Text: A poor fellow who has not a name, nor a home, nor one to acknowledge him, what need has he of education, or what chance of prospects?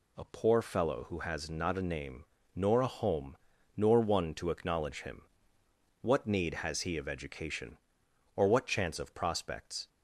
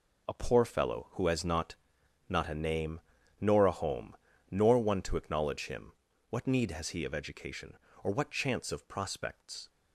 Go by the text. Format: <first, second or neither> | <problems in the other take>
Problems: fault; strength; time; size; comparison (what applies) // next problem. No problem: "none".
first | says "not" twice; at 2.2 s